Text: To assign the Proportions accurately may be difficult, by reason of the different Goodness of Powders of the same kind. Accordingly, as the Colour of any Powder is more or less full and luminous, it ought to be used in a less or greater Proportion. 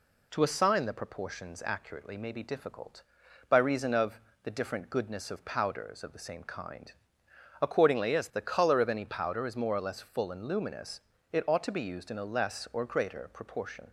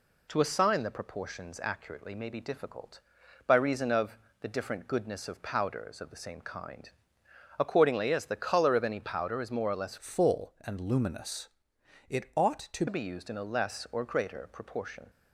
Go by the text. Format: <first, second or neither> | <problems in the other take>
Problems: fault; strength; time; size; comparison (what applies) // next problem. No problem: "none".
first | pauses between "of" and "the"; slight; at 4.1 s; 0.22 s long; slight in the first // changes voice from "full" to "to"; from 9.9 to 12.8 s; 2.9 s long